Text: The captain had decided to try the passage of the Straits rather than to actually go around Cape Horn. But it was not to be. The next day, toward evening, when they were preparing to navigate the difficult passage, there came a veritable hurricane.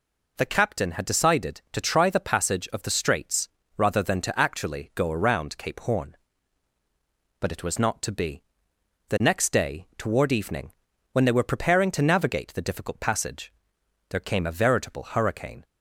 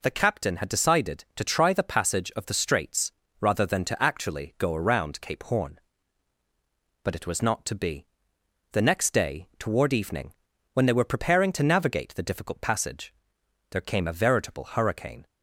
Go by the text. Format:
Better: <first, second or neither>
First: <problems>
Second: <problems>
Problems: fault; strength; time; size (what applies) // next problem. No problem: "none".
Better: neither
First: pauses between "Straits" and "rather"; slight; at 3.4 s; 0.30 s long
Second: pauses between "Straits" and "rather"; slight; at 3.1 s; 0.30 s long